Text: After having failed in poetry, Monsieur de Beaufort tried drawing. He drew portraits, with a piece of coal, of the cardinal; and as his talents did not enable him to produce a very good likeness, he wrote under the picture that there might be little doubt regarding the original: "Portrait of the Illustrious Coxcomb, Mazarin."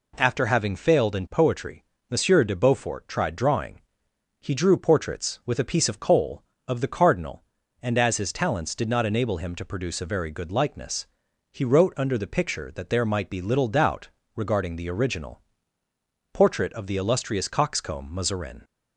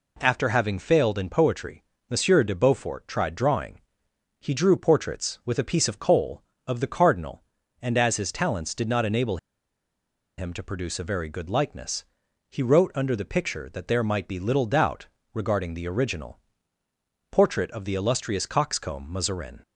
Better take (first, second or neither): first